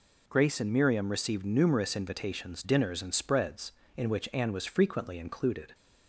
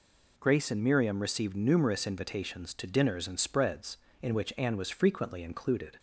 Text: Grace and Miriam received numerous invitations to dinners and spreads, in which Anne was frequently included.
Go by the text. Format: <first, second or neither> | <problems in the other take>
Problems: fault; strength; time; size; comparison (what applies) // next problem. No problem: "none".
second | skips "to"; at 2.6 s